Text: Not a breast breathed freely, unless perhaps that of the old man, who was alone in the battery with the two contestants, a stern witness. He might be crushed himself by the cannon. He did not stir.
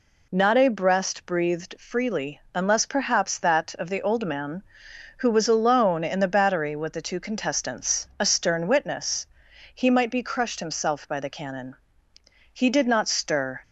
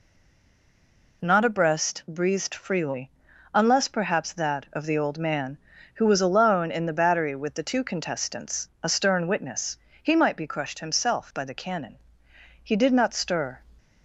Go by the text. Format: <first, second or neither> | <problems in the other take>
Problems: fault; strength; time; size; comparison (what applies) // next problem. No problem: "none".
first | stays silent before the first word; noticeable; until 1.2 s; 1.2 s long